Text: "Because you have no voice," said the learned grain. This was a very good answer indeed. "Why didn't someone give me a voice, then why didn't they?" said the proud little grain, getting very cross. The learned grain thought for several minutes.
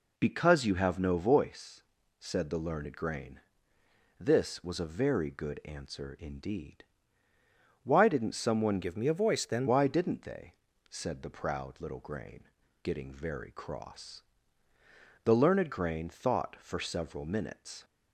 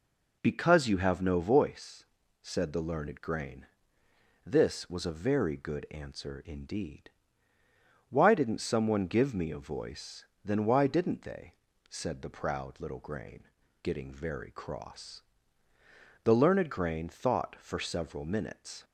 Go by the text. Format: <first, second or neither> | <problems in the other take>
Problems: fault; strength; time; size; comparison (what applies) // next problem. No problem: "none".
second | changes voice from "give" to "then"; from 8.8 to 9.6 s; 0.8 s long